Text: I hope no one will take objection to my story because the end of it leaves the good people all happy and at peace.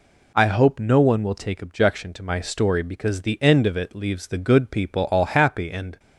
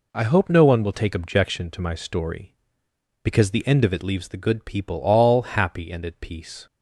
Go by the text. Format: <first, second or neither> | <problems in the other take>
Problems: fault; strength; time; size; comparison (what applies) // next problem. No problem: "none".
second | stops before "at peace"; at 5.9 s